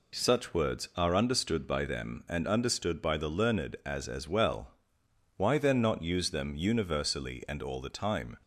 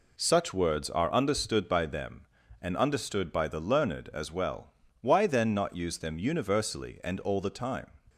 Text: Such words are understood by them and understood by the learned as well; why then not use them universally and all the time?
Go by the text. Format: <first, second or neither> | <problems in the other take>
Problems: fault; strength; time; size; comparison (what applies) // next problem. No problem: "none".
second | says "as" twice; at 4.0 s